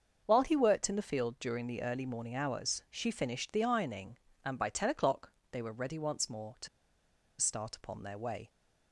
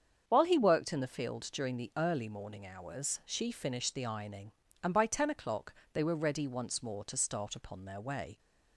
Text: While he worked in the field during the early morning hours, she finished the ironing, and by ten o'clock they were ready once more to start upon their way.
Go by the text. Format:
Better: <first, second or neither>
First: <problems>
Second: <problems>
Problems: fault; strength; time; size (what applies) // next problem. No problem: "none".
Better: second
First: starts louder than the rest; until 1.2 s; 6.5 dB // pauses between "o'clock" and "they"; slight; at 5.3 s; 0.18 s long // pauses between "to" and "start"; noticeable; at 6.6 s; 0.73 s long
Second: starts louder than the rest; strong; until 1.2 s; 7.5 dB // pauses between "o'clock" and "they"; slight; at 5.7 s; 0.18 s long